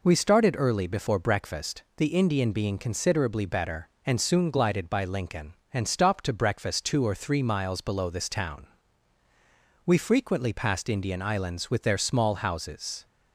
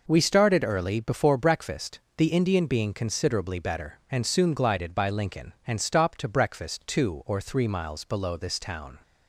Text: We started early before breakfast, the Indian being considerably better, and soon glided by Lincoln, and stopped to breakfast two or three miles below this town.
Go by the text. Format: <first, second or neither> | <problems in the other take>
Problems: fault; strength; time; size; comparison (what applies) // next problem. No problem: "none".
second | goes on to say "We frequently passed Indian islands with their small houses"; strong; from 9.8 s on; 3.2 s long